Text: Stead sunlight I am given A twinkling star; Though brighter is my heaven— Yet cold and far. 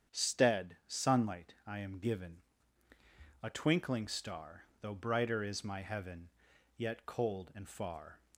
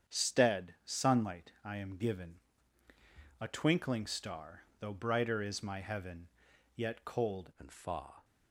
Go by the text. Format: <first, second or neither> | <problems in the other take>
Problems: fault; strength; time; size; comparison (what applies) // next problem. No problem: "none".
first | starts louder than the rest; strong; until 1.1 s; 8 dB; strong in the first // pauses between "given" and "A"; at 2.3 s; 1.0 s long; also in the first // changes voice at "and"; from 7.5 s on; 0.7 s long